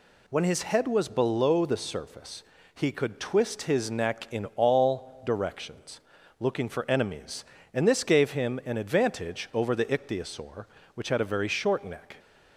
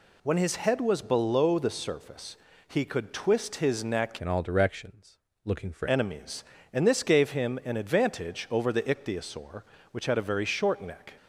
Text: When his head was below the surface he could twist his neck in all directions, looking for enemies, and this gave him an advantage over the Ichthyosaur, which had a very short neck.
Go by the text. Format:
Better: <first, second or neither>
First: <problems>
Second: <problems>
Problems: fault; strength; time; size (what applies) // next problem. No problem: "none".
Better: first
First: pauses between "surface" and "he"; slight; at 2.4 s; 0.32 s long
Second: pauses between "surface" and "he"; slight; at 2.3 s; 0.32 s long // changes voice from "in" to "for"; from 4.2 to 5.8 s; 1.6 s long